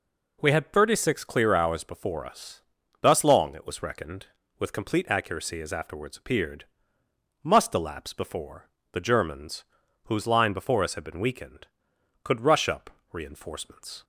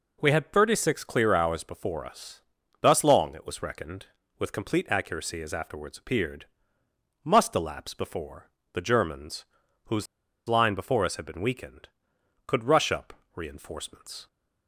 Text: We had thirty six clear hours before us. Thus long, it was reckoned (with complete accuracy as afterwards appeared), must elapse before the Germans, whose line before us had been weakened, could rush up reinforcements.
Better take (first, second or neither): first